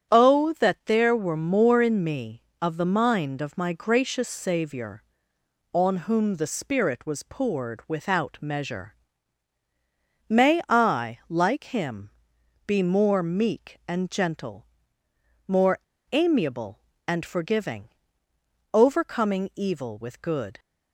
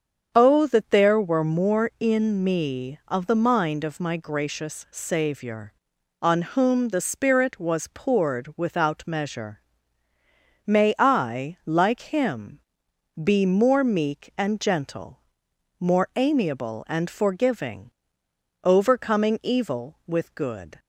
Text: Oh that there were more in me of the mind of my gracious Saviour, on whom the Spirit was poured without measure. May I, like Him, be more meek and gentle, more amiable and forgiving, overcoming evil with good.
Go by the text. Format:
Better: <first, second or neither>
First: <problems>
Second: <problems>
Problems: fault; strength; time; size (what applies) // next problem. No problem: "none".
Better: second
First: starts louder than the rest; strong; until 1.1 s; 7.5 dB // pauses between "more" and "amiable"; slight; at 15.7 s; 0.32 s long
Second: starts louder than the rest; until 1.3 s; 7 dB